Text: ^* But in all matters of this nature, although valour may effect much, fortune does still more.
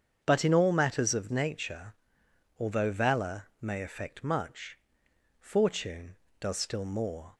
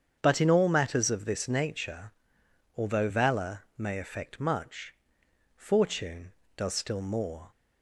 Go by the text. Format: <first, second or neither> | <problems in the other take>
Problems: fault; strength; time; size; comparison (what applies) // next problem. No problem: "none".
second | starts louder than the rest; strong; until 1.2 s; 7.5 dB; strong in the second // skips "this"; at 1.2 s